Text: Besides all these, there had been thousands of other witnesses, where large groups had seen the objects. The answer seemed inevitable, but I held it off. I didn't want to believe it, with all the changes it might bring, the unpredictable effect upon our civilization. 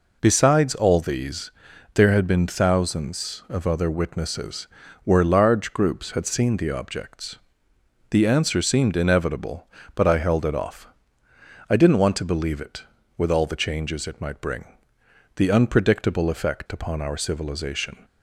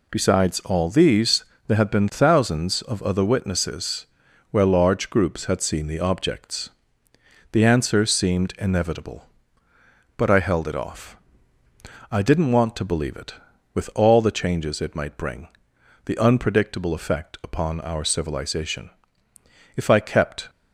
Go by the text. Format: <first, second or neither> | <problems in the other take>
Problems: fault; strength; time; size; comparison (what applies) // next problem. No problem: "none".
first | goes on to say "If I kept"; noticeable; from 19.7 s on; 0.74 s long